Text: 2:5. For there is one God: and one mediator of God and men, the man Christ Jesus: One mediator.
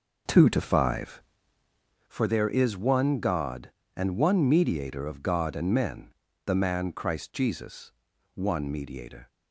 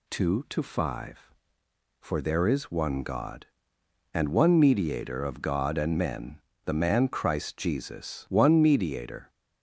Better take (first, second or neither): second